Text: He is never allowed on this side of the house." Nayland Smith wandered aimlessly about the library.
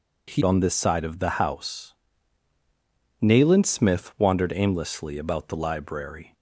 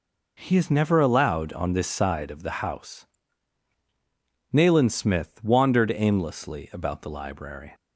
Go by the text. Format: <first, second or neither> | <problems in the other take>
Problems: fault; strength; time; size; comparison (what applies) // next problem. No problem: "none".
second | skips "is never allowed"; at 0.4 s